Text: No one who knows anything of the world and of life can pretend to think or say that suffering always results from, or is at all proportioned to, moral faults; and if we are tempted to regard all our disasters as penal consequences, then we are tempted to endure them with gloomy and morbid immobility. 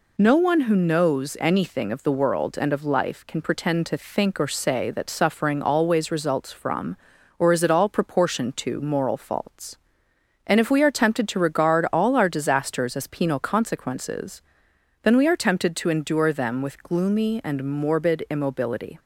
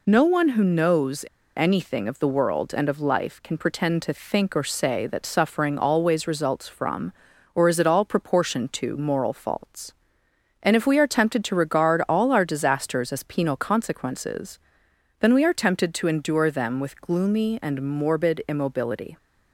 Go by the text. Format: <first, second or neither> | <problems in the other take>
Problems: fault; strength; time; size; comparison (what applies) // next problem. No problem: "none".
first | pauses between "knows" and "anything"; slight; at 1.2 s; 0.33 s long